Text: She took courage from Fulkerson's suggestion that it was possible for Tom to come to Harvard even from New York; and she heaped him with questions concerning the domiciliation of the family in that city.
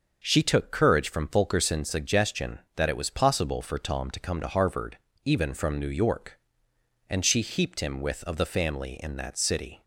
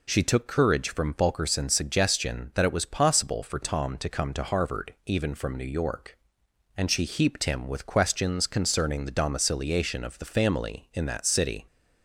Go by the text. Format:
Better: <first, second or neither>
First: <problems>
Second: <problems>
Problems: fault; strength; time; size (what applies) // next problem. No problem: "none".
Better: second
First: starts louder than the rest; until 1.2 s; 6 dB // pauses between "Harvard" and "even"; slight; at 4.9 s; 0.28 s long // skips "questions concerning the domiciliation"; at 8.2 s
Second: none